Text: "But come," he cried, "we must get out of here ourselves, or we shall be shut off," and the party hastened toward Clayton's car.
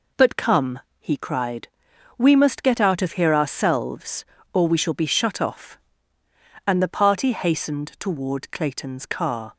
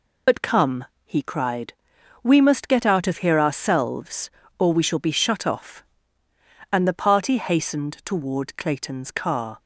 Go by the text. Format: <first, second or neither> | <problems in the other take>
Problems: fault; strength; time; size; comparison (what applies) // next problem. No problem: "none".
first | loses the start of "But"; at 0.2 s; 70 ms